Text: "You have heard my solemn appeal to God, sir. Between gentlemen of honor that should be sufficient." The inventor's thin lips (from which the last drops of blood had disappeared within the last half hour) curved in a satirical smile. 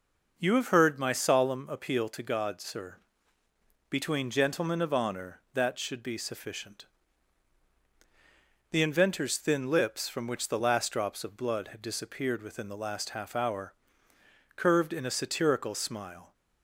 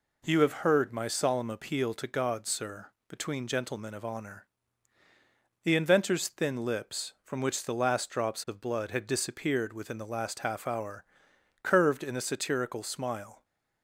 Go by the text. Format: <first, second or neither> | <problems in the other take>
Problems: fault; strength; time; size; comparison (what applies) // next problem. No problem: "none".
first | skips "that should be sufficient"; at 5.0 s